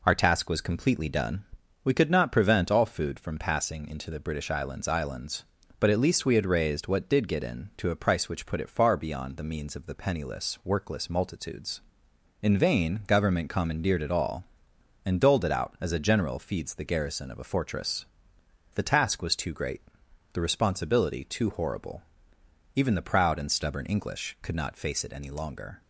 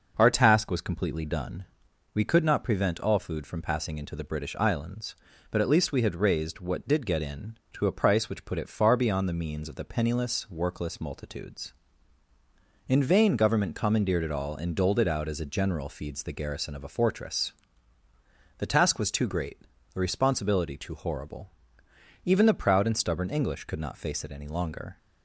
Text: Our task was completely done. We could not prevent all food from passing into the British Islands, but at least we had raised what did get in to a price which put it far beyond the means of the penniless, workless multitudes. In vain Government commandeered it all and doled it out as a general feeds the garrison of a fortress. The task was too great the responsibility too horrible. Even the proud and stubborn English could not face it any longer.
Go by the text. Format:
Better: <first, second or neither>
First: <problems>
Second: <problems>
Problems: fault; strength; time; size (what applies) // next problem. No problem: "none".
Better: second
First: says "Islands" twice; at 4.8 s // pauses between "great" and "the"; noticeable; at 19.8 s; 0.52 s long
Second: pauses between "great" and "the"; slight; at 19.5 s; 0.36 s long